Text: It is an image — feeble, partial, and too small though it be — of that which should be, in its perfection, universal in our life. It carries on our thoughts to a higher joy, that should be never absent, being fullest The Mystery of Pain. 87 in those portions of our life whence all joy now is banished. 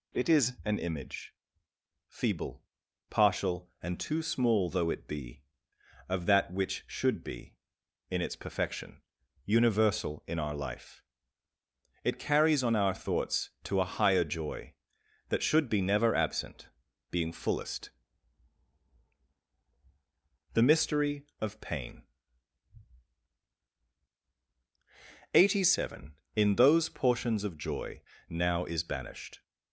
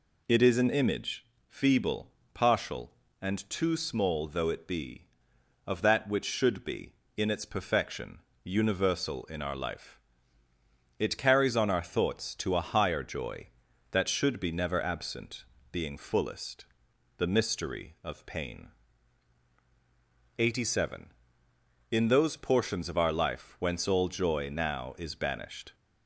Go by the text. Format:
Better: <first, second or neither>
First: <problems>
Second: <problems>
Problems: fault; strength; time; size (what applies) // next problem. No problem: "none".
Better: second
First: pauses between "fullest" and "The"; strong; at 17.8 s; 2.6 s long // skips "our life whence all"; at 27.5 s // pauses between "joy" and "now"; slight; at 28.0 s; 0.26 s long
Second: pauses between "fullest" and "The"; noticeable; at 16.6 s; 0.54 s long